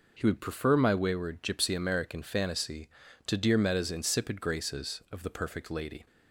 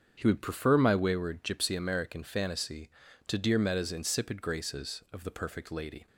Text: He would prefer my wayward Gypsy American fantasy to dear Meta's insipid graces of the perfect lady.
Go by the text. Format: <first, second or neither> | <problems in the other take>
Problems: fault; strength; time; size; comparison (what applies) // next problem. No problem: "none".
first | starts louder than the rest; strong; until 1.5 s; 7.5 dB